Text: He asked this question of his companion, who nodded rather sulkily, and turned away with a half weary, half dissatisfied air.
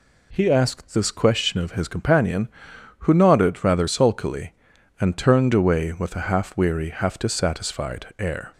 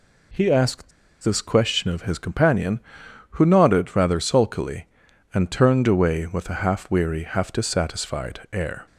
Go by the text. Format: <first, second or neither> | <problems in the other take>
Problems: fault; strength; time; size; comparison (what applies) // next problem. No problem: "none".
first | pauses between "asked" and "this"; slight; at 0.9 s; 0.32 s long